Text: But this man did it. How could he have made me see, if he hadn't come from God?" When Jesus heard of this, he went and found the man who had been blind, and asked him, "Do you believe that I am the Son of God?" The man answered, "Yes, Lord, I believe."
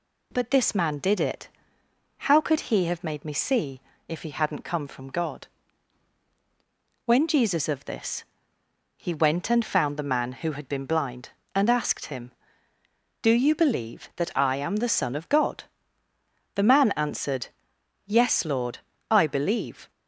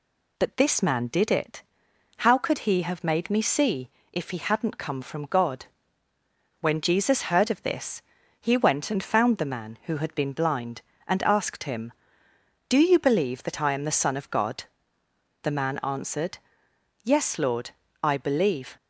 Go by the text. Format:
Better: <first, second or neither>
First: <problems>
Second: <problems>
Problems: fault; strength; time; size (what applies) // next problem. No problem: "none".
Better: second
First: skips "heard"; at 7.6 s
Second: none